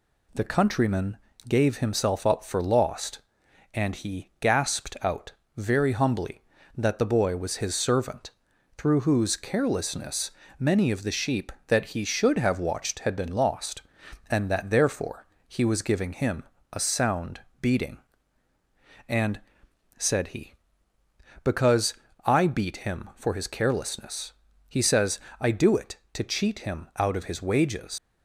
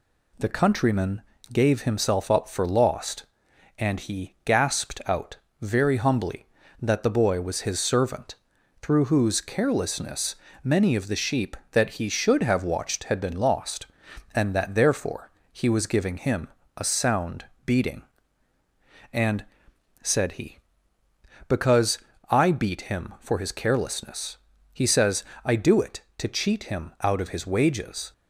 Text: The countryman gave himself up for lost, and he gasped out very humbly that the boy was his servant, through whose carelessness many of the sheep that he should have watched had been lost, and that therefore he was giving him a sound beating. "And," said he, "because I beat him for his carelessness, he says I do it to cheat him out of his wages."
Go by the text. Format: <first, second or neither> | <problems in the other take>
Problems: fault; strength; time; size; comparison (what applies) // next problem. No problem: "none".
second | pauses between "countryman" and "gave"; slight; at 1.1 s; 0.30 s long; slight in the second // pauses between "out" and "very"; slight; at 5.3 s; 0.24 s long; slight in the second // pauses between "carelessness" and "many"; slight; at 10.2 s; 0.28 s long; slight in the second // pauses between "therefore" and "he"; slight; at 15.2 s; 0.22 s long; slight in the second // pauses between "him" and "a"; slight; at 16.4 s; 0.28 s long; slight in the second // pauses between "sound" and "beating"; slight; at 17.3 s; 0.20 s long; slight in the second // pauses between "because" and "I"; slight; at 21.9 s; 0.30 s long; slight in the second // pauses between "says" and "I"; slight; at 25.1 s; 0.22 s long; slight in the second // leaves "wages" unfinished; at 27.9 s; 95 ms